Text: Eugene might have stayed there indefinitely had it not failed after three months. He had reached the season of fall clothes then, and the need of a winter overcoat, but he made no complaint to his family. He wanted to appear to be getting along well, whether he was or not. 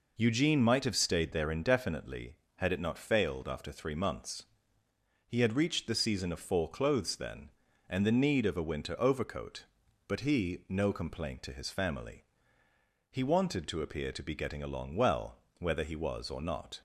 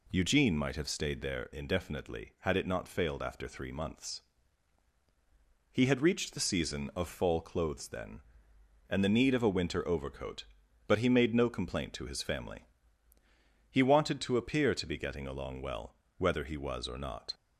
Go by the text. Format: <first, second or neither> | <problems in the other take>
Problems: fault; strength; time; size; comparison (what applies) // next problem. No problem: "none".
second | skips "made"; at 10.6 s